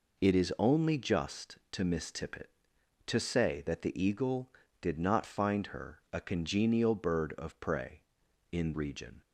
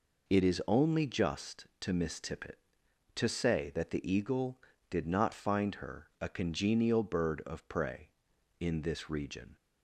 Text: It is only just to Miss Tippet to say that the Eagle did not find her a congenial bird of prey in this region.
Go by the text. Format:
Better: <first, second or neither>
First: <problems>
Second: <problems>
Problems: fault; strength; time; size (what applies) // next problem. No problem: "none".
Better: second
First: skips "this"; at 8.7 s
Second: none